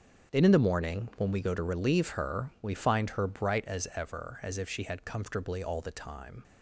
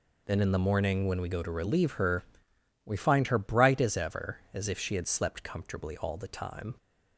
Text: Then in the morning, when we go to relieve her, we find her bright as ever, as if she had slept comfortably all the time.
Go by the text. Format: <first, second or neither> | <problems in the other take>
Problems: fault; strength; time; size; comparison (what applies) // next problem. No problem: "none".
second | starts louder than the rest; until 1.3 s; 7 dB // skips "slept"; at 5.0 s